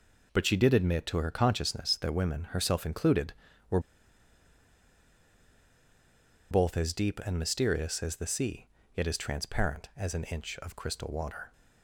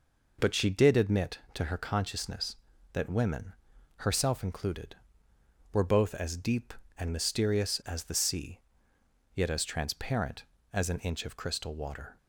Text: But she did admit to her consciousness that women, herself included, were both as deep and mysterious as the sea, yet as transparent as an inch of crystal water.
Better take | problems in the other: second | pauses between "were" and "both"; strong; at 3.7 s; 2.7 s long

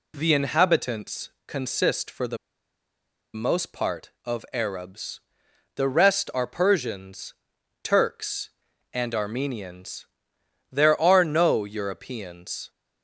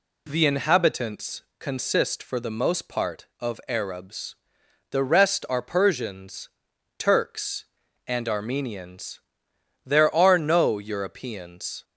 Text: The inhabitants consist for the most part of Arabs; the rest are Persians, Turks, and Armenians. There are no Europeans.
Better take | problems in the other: second | pauses between "the" and "most"; at 2.3 s; 0.98 s long

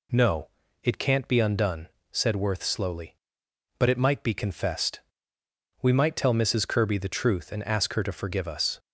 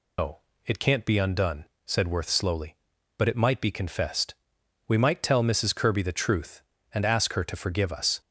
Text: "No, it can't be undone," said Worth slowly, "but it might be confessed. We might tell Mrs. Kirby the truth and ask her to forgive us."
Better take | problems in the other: first | loses the start of "No"; at 0.1 s; 145 ms

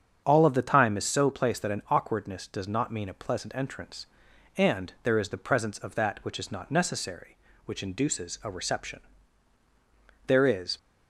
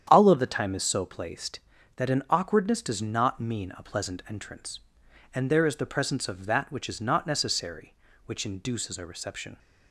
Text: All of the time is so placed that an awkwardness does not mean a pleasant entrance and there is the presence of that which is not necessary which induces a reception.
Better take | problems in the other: second | starts louder than the rest; strong; until 1.2 s; 7.5 dB; strong in the second // goes on to say "There is"; from 10.2 s on; 0.50 s long

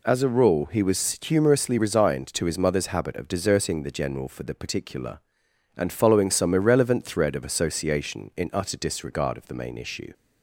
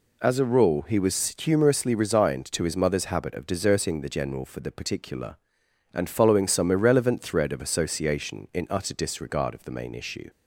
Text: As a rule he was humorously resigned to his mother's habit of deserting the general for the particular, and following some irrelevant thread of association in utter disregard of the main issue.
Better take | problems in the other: neither | none

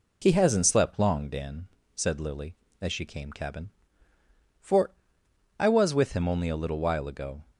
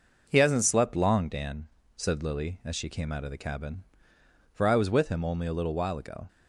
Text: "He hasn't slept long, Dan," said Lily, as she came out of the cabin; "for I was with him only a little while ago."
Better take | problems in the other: second | skips "out of the"; at 3.3 s // pauses between "for" and "I"; noticeable; at 4.9 s; 0.68 s long

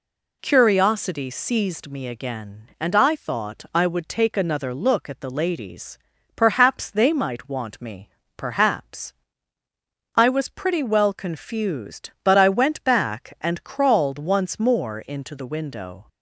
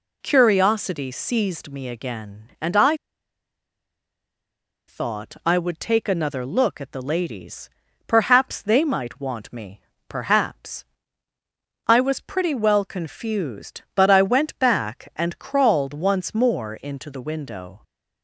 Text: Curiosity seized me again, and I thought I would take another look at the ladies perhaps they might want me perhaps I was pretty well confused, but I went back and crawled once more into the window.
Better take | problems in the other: first | pauses between "I" and "thought"; strong; at 2.9 s; 1.9 s long // pauses between "ladies" and "perhaps"; at 7.6 s; 0.40 s long; also in the first // pauses between "me" and "perhaps"; slight; at 9.7 s; 0.30 s long; slight in the first // pauses between "perhaps" and "I"; at 10.8 s; 1.0 s long; also in the first

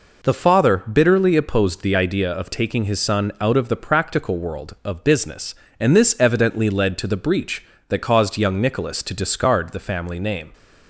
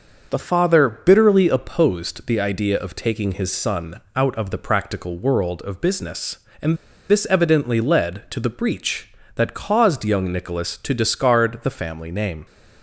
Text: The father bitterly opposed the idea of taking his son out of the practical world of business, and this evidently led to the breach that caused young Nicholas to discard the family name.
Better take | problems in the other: first | starts louder than the rest; until 1.3 s; 6.5 dB // pauses between "and" and "this"; slight; at 6.7 s; 0.33 s long

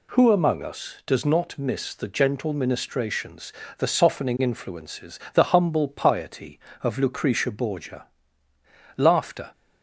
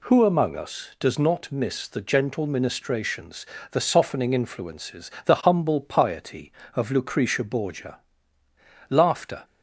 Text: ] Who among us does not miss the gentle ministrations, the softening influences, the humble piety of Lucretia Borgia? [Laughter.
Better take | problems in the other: neither | none

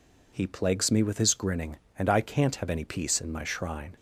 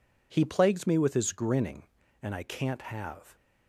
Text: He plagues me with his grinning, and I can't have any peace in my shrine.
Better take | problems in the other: first | stops before "any peace in my shrine"; at 3.3 s

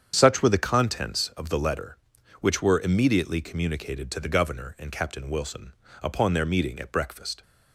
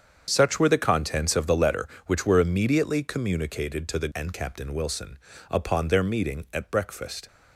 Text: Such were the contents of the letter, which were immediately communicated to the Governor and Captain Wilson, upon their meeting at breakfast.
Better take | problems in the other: first | starts louder than the rest; strong; until 1.2 s; 7.5 dB; strong in the first // skips "Governor"; at 4.1 s

